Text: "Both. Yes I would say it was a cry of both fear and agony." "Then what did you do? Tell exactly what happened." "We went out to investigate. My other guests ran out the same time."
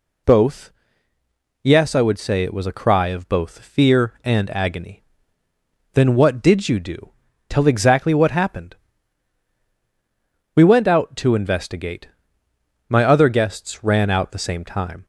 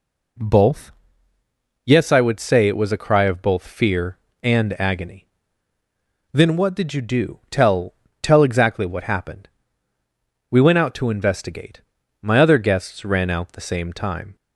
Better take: first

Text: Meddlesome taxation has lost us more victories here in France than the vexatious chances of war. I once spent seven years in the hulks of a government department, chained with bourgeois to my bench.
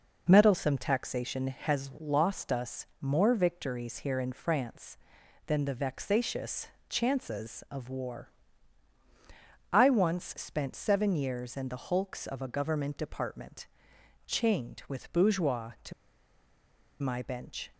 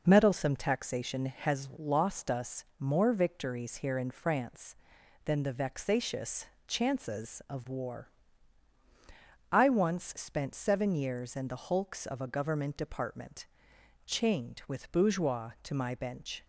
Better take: second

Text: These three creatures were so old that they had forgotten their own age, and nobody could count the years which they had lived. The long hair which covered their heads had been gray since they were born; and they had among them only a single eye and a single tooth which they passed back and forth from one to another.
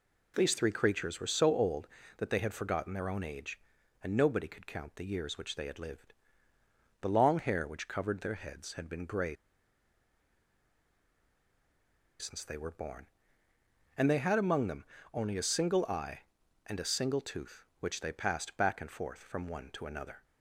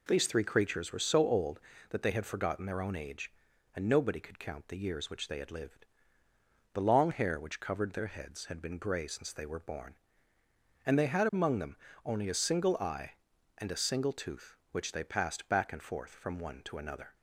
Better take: second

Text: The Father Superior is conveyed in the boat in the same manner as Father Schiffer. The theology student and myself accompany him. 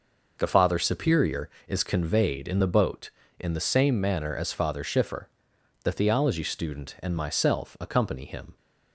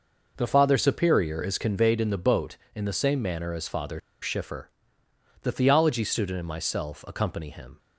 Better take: first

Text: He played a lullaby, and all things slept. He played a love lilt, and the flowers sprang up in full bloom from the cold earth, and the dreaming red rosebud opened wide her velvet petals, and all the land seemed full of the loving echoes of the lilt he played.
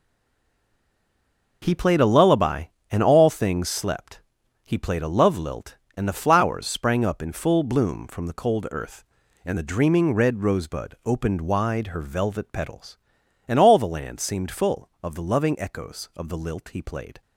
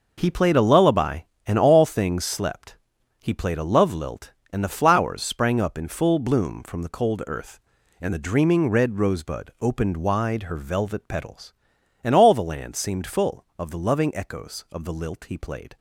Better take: second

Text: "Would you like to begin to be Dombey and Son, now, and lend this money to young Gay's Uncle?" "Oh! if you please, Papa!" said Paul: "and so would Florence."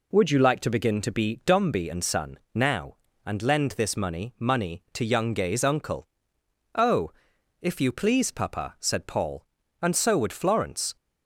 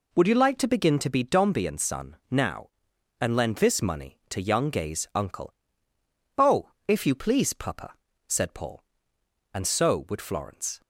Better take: second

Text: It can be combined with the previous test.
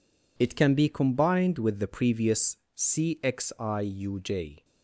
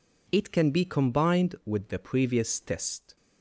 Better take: second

